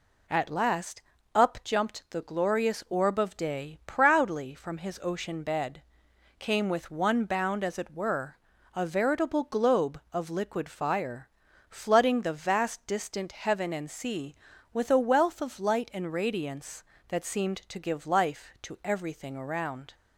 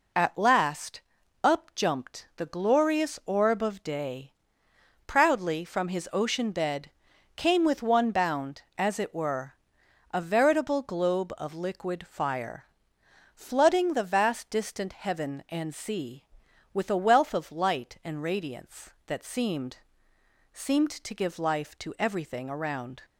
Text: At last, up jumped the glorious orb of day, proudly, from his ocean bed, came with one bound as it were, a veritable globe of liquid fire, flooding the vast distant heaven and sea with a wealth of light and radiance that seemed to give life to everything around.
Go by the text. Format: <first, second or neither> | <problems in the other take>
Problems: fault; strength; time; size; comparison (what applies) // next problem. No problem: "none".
first | says "seemed" twice; at 20.5 s